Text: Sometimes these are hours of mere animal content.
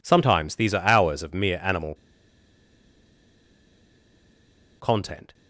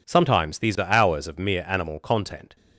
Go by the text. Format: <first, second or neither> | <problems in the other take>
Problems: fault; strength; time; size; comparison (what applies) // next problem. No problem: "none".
second | pauses between "animal" and "content"; strong; at 1.9 s; 2.8 s long